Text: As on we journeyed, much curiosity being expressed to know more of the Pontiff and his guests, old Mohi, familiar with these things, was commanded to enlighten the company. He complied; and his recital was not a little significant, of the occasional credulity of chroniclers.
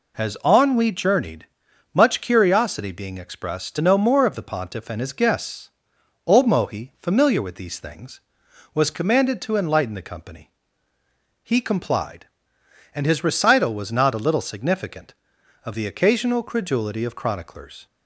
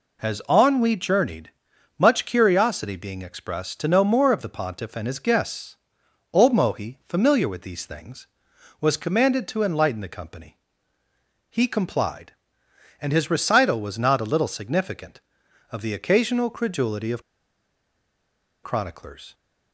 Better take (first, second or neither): first